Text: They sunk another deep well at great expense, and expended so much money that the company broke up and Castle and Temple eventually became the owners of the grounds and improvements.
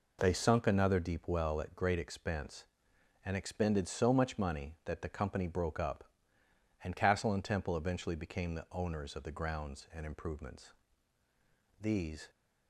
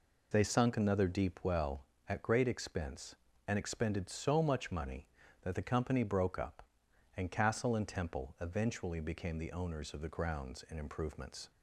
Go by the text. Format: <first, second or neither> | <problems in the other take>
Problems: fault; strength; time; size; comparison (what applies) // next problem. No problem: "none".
second | goes on to say "These"; from 11.7 s on; 0.50 s long